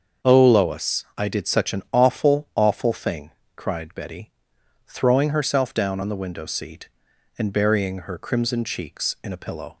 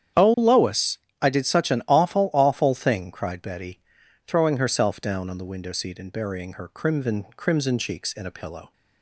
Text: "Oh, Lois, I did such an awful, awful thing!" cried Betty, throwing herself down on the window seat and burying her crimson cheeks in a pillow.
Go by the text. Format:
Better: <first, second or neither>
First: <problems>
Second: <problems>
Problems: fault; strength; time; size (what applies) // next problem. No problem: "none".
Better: first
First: starts louder than the rest; until 1.3 s; 6.5 dB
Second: starts louder than the rest; strong; until 1.4 s; 9 dB // says "crimson" twice; at 7.3 s